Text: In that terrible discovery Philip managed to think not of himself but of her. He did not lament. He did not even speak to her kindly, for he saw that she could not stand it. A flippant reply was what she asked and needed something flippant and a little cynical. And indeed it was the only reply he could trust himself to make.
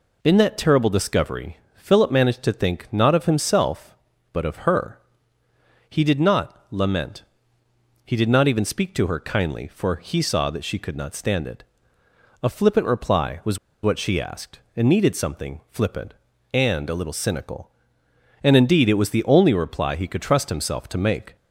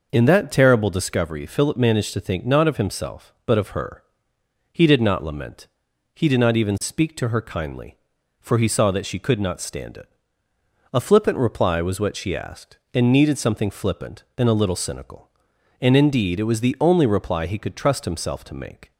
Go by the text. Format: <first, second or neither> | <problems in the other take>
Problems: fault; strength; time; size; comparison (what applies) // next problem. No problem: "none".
second | pauses between "discovery" and "Philip"; slight; at 1.5 s; 0.20 s long // pauses between "was" and "what"; slight; at 13.5 s; 0.25 s long